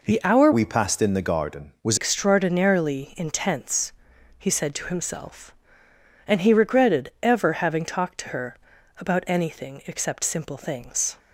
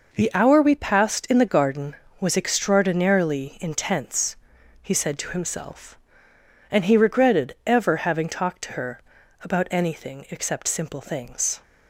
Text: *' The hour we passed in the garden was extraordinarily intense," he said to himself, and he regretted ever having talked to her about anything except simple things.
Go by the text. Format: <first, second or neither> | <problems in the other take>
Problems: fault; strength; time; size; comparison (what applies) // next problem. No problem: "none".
second | changes voice from "we" to "was"; from 0.5 to 1.9 s; 1.4 s long // pauses between "her" and "about"; at 8.5 s; 0.42 s long; also in the second